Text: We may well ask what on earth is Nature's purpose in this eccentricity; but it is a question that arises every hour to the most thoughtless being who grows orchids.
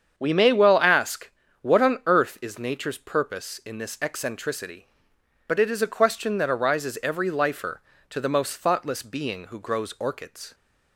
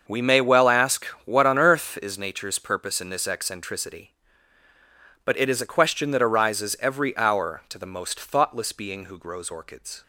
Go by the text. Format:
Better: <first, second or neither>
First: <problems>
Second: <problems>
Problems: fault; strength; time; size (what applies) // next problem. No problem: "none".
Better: second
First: starts louder than the rest; strong; until 1.2 s; 7.5 dB // pauses between "ask" and "what"; slight; at 1.3 s; 0.30 s long // says "lifer" for "hour"; at 7.2 s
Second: starts louder than the rest; until 1.2 s; 6.5 dB // pauses between "ask" and "what"; slight; at 1.0 s; 0.20 s long